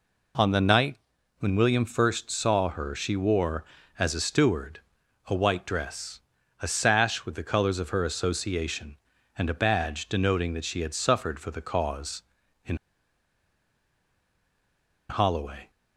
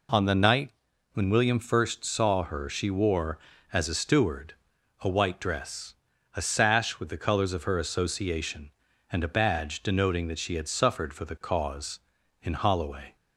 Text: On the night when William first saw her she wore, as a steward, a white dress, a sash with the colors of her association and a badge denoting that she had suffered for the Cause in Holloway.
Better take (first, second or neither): second